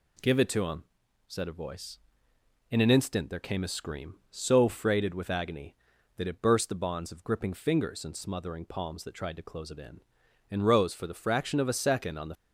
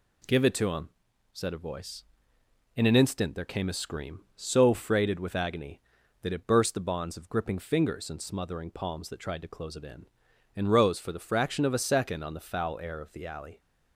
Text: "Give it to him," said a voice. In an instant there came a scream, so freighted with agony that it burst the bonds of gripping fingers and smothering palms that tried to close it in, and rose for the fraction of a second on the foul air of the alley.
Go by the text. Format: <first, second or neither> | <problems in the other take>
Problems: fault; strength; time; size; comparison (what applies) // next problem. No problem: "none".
second | stops before "foul air of the alley"; at 12.3 s